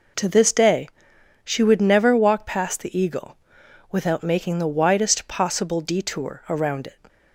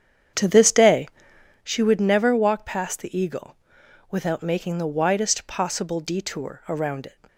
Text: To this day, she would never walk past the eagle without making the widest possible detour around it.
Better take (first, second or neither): first